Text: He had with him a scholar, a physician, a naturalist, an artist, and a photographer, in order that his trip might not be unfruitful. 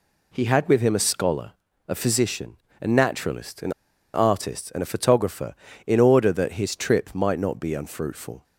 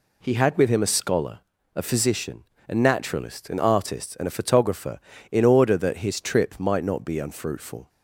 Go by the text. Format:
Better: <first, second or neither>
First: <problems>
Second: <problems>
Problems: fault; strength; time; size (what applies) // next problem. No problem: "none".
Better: second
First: pauses between "an" and "artist"; at 3.7 s; 0.43 s long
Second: none